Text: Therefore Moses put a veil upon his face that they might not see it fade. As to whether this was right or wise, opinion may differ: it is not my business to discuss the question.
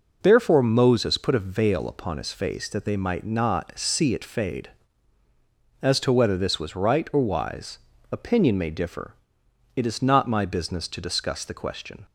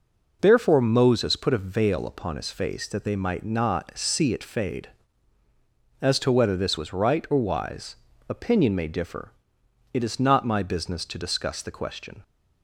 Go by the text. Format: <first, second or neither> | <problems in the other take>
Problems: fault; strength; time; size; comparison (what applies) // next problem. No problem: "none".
neither | none